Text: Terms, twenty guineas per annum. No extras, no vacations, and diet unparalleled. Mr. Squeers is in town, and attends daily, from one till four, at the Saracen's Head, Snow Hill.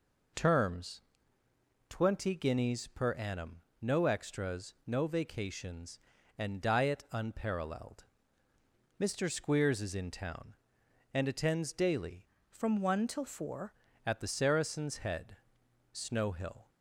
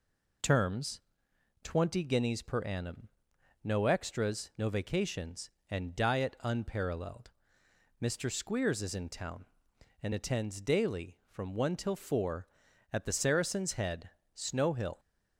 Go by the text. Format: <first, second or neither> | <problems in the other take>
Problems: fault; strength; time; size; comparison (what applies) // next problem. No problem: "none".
second | changes voice from "from" to "four"; from 12.4 to 13.7 s; 1.3 s long